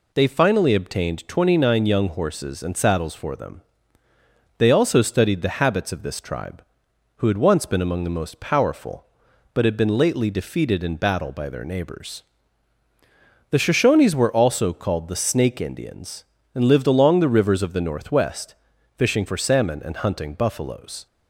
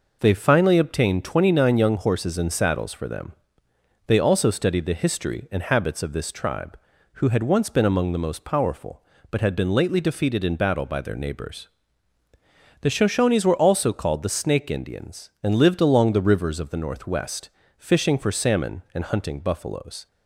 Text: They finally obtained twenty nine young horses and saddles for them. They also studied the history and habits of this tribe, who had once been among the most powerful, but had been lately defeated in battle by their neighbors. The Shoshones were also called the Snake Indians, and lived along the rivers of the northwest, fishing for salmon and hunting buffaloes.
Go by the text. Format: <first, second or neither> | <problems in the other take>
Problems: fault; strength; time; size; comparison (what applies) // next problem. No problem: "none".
second | skips "history and"; at 5.6 s